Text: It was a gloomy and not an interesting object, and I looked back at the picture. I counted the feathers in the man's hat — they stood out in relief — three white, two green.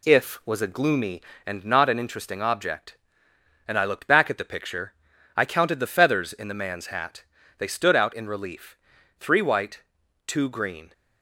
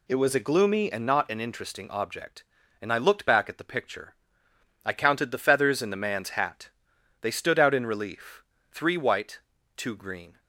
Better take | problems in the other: second | says "If" for "It"; at 0.0 s

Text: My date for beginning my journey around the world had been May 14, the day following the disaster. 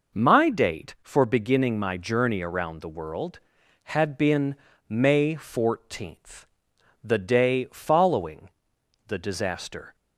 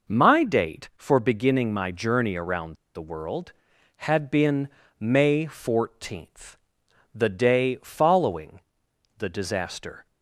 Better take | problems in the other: first | pauses between "around" and "the"; slight; at 2.7 s; 0.19 s long // pauses between "been" and "May"; slight; at 4.6 s; 0.30 s long; slight in the first // pauses between "following" and "the"; noticeable; at 8.5 s; 0.60 s long; noticeable in the first

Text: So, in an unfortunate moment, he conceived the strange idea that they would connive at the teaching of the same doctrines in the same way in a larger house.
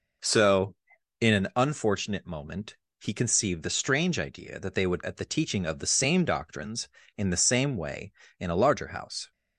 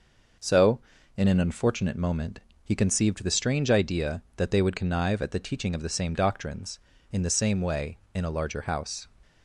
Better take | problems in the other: second | skips "connive"; at 5.0 s

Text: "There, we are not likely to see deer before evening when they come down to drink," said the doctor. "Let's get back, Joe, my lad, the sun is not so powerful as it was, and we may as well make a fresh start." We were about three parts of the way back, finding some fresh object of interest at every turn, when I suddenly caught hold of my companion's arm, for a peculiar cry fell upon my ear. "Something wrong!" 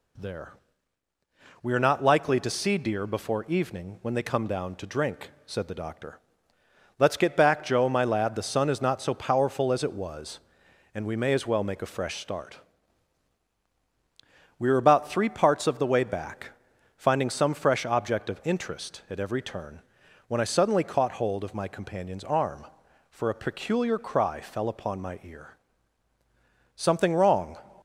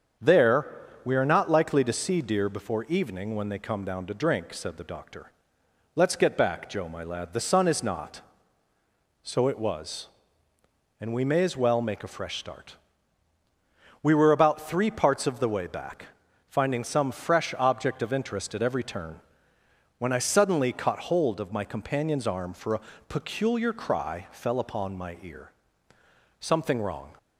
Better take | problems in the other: first | starts louder than the rest; strong; until 1.5 s; 7.5 dB // skips "powerful as"; at 9.4 s // pauses between "a" and "peculiar"; slight; at 22.8 s; 0.26 s long

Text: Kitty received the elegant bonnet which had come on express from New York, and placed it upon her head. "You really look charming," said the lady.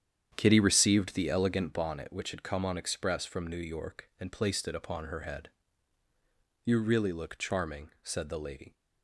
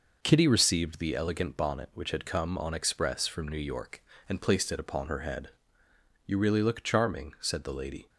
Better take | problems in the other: second | starts louder than the rest; strong; until 1.8 s; 9 dB

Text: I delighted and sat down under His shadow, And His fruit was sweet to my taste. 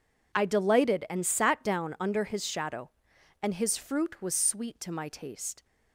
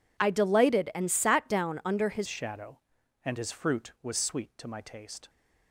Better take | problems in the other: first | changes voice at "shadow"; from 2.2 s on; 3.0 s long

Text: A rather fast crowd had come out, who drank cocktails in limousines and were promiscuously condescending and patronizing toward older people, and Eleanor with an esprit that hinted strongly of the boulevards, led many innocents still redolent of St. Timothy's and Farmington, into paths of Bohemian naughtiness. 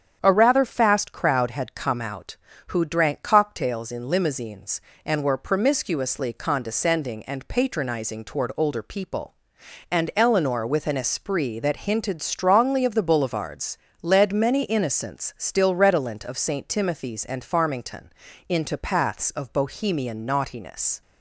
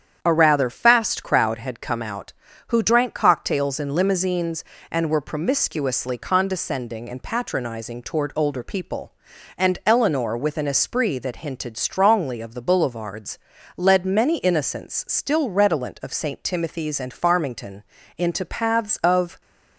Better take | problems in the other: first | starts louder than the rest; strong; until 1.2 s; 8.5 dB; strong in the first // stops before "Bohemian naughtiness"; at 19.4 s

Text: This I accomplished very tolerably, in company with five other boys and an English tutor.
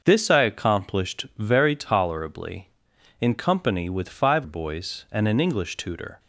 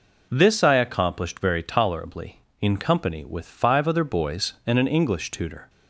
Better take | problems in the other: second | starts louder than the rest; until 1.0 s; 6 dB // skips "other"; at 4.4 s

